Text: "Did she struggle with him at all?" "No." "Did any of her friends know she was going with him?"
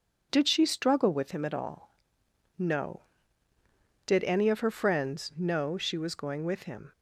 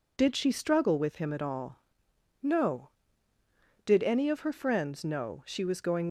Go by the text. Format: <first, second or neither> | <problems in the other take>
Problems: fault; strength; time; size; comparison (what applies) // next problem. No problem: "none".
first | stops before "with him"; at 6.0 s